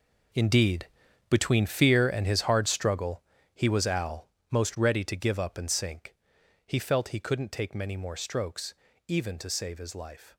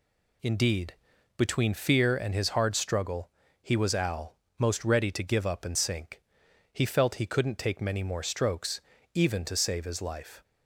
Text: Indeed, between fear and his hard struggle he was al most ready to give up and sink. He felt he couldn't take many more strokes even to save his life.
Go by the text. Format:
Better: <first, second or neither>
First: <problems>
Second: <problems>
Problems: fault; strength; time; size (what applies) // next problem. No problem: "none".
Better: second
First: gets quieter; strong; throughout; 13 dB // pauses between "struggle" and "he"; slight; at 3.2 s; 0.32 s long // pauses between "al" and "most"; slight; at 4.2 s; 0.20 s long // pauses between "strokes" and "even"; slight; at 8.7 s; 0.34 s long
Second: pauses between "struggle" and "he"; slight; at 3.2 s; 0.32 s long // pauses between "al" and "most"; slight; at 4.3 s; 0.20 s long // pauses between "strokes" and "even"; slight; at 8.8 s; 0.34 s long